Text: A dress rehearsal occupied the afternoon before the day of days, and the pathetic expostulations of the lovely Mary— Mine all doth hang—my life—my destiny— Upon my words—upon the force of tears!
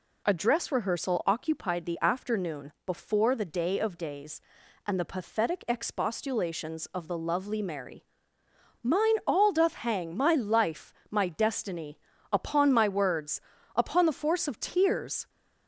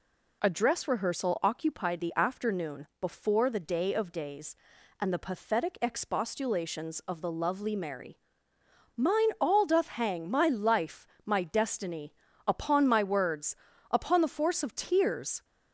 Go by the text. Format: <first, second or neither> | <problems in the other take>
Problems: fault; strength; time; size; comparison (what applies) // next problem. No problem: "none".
neither | none